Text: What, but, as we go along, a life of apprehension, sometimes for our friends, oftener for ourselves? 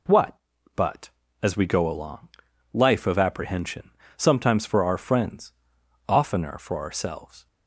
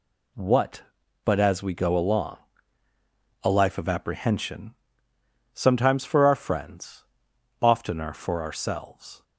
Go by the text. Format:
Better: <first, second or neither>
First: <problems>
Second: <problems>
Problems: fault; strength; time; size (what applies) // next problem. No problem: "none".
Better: second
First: skips "a"; at 2.5 s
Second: none